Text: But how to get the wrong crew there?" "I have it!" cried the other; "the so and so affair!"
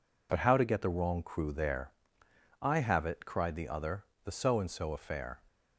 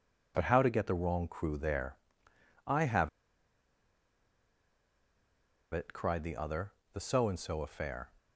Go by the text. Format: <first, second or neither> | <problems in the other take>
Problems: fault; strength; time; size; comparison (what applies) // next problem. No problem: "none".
first | pauses between "have" and "it"; strong; at 3.0 s; 2.6 s long